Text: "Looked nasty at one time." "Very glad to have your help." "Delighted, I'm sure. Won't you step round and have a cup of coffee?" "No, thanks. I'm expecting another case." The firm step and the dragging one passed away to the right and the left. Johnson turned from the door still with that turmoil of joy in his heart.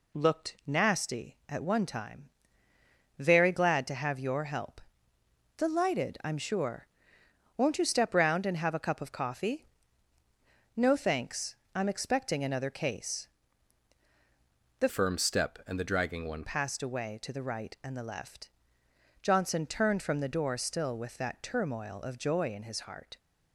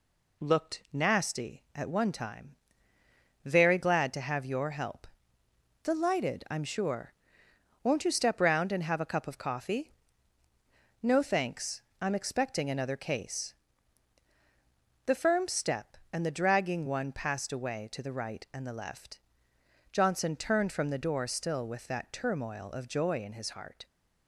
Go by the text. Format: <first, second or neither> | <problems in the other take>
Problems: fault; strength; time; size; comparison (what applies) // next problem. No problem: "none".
second | changes voice from "firm" to "one"; from 14.8 to 16.4 s; 1.6 s long